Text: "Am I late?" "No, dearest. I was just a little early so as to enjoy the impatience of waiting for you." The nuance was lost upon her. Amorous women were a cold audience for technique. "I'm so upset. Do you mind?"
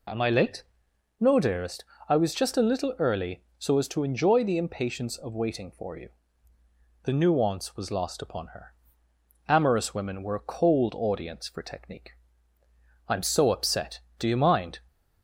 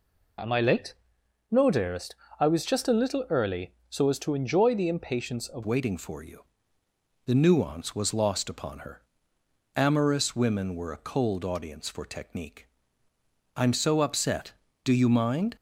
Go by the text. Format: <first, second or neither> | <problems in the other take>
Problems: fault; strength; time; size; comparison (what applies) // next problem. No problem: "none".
first | changes voice at "waiting"; from 5.6 s on; 9.9 s long